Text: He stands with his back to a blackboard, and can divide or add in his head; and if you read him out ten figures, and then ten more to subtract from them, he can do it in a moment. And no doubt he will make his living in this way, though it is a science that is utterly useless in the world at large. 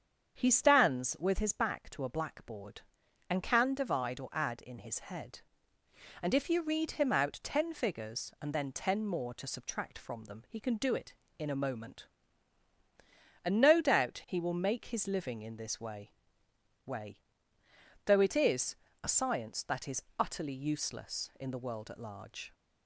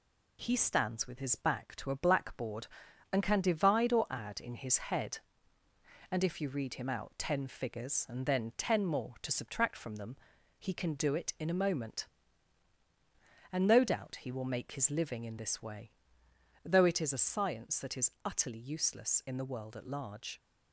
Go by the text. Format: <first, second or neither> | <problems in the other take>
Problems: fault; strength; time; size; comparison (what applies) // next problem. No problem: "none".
second | starts louder than the rest; strong; until 1.3 s; 7.5 dB // says "way" twice; at 16.8 s // pauses between "is" and "a"; slight; at 18.7 s; 0.28 s long